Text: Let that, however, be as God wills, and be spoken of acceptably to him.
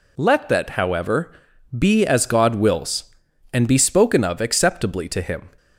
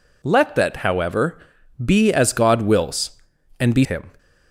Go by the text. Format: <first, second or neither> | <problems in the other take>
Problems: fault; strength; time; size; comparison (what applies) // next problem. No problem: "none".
first | skips "spoken of acceptably to"; at 3.8 s